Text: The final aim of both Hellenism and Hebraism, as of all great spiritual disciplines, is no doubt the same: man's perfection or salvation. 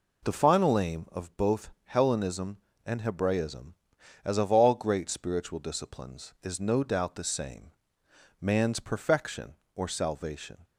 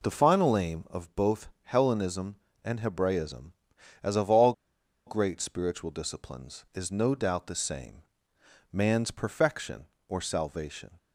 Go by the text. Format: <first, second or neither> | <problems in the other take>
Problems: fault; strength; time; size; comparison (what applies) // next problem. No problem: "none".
first | pauses between "all" and "great"; noticeable; at 4.5 s; 0.54 s long